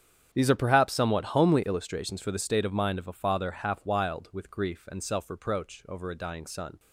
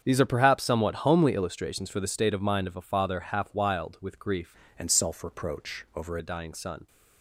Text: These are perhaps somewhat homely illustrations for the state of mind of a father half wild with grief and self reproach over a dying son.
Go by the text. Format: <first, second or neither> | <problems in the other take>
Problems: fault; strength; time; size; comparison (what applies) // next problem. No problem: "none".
first | starts louder than the rest; strong; until 1.0 s; 7.5 dB; strong in the first // changes voice from "and" to "over"; from 4.7 to 6.1 s; 1.4 s long